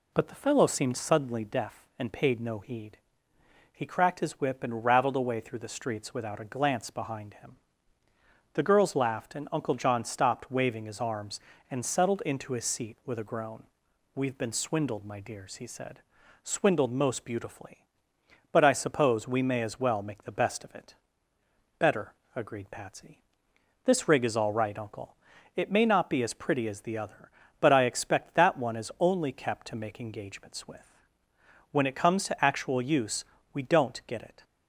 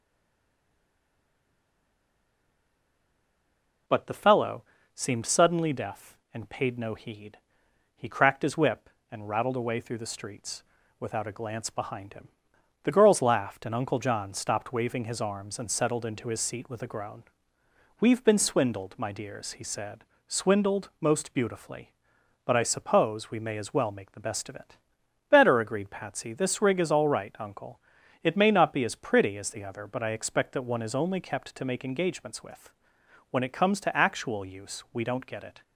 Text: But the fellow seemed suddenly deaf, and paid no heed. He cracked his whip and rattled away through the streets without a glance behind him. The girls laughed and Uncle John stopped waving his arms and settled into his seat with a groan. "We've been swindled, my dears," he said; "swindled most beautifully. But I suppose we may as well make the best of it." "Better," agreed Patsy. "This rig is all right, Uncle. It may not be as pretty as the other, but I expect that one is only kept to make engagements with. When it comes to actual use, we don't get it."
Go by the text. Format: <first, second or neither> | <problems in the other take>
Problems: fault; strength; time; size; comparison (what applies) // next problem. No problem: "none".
first | stays silent before the first word; strong; until 3.8 s; 3.8 s long // pauses between "fellow" and "seemed"; slight; at 4.6 s; 0.30 s long // pauses between "streets" and "without"; at 10.6 s; 0.38 s long